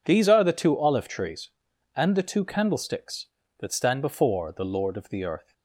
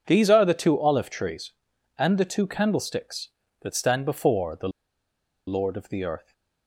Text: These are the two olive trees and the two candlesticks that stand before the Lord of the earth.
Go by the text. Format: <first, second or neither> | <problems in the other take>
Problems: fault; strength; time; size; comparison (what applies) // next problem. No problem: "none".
first | pauses between "the" and "Lord"; noticeable; at 4.6 s; 0.78 s long